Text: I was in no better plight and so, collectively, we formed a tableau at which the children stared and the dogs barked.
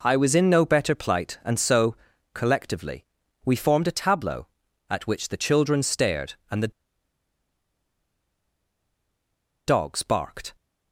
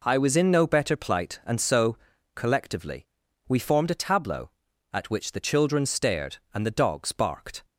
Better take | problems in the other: second | pauses between "the" and "dogs"; strong; at 6.7 s; 2.9 s long

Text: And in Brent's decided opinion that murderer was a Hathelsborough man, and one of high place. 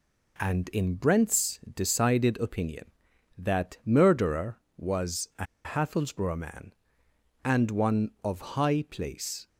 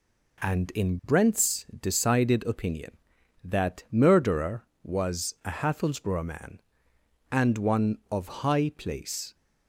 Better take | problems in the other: second | pauses between "Brent's" and "decided"; slight; at 1.5 s; 0.16 s long; slight in the second // pauses between "a" and "Hathelsborough"; slight; at 5.4 s; 0.20 s long

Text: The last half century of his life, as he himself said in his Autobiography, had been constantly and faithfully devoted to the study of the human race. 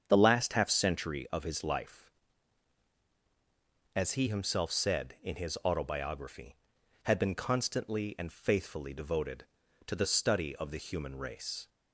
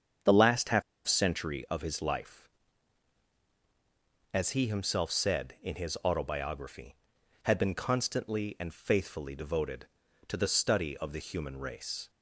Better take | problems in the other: first | starts louder than the rest; strong; until 1.4 s; 7.5 dB; strong in the first // pauses between "half" and "century"; slight; at 0.8 s; 0.25 s long

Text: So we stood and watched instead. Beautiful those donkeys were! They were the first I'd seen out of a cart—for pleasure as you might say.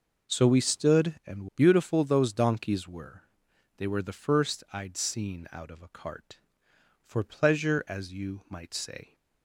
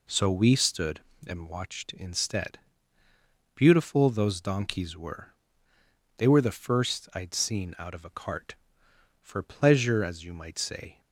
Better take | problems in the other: second | skips "watched instead"; at 1.5 s

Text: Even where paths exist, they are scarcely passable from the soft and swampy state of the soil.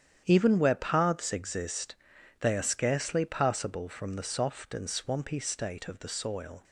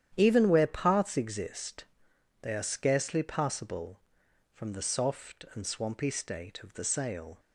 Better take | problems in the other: first | starts louder than the rest; strong; until 1.1 s; 10 dB; strong in the first // says "sail" for "soil"; at 6.8 s

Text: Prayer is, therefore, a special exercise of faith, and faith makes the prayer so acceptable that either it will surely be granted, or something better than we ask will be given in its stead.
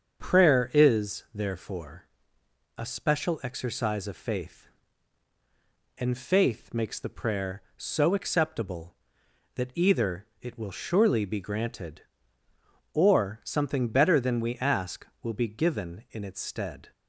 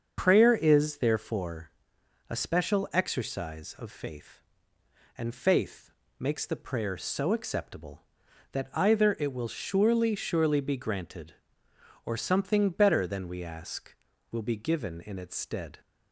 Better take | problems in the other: first | starts louder than the rest; until 1.1 s; 6.5 dB; also in the first // pauses between "faith" and "makes"; slight; at 5.9 s; 0.28 s long // says "surely" twice; at 10.1 s

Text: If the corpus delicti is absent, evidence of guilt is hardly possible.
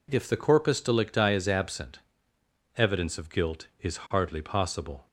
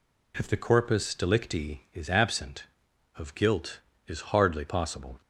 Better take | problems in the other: first | skips "evidence"; at 2.9 s

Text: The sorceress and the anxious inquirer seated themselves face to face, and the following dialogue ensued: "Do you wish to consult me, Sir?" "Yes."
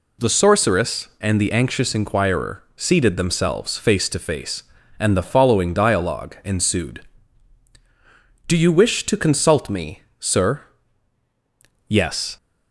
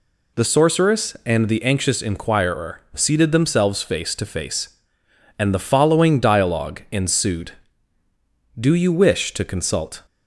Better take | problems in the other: first | stops before "me Sir Yes"; at 10.0 s

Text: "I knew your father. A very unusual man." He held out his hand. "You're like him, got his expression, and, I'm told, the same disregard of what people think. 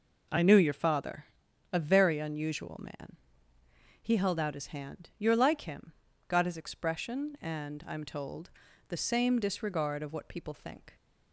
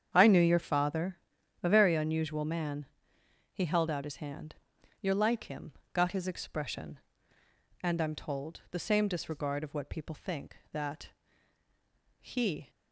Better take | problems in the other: first | starts louder than the rest; strong; until 1.1 s; 8 dB // goes on to say "That he"; strong; from 10.7 s on; 1.9 s long

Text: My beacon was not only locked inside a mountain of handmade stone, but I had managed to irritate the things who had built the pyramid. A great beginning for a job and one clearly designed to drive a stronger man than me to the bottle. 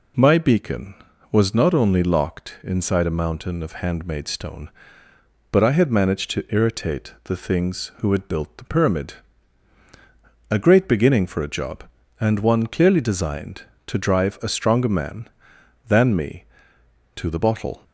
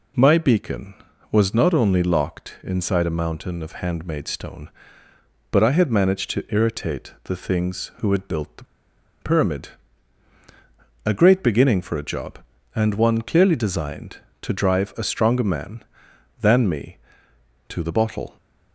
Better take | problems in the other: first | pauses between "the" and "pyramid"; noticeable; at 8.6 s; 0.57 s long

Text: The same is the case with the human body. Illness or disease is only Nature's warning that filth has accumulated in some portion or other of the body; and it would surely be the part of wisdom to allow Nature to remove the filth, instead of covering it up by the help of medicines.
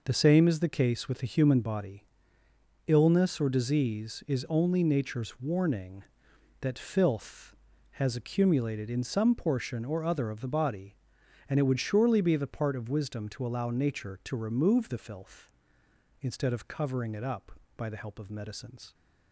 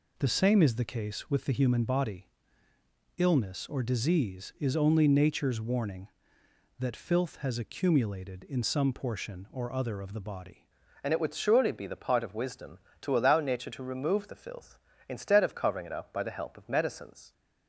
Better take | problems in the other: first | changes voice at "and"; from 11.0 s on; 6.3 s long

